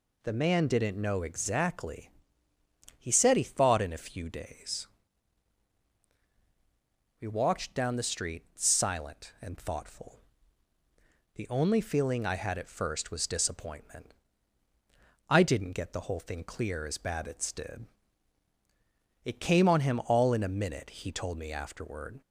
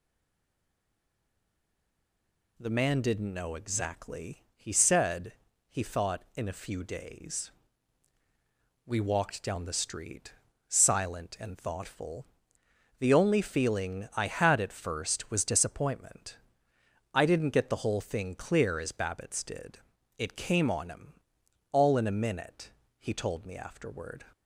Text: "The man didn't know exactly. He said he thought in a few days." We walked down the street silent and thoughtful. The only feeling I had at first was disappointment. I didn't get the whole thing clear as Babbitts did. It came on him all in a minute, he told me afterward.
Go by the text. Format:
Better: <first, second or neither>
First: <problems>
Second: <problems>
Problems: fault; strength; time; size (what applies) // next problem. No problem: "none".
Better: first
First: none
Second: stays silent before the first word; strong; until 2.5 s; 2.5 s long // pauses between "said" and "he"; slight; at 5.3 s; 0.36 s long // pauses between "street" and "silent"; slight; at 10.3 s; 0.36 s long // pauses between "him" and "all"; noticeable; at 21.2 s; 0.50 s long